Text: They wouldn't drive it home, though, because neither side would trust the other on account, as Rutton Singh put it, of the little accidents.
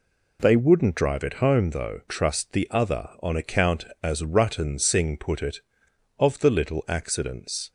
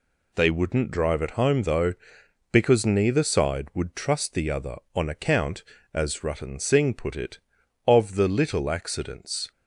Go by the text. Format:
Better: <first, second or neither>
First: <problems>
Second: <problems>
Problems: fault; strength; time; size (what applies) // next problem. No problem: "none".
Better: second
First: skips "because neither side would"; at 2.0 s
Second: none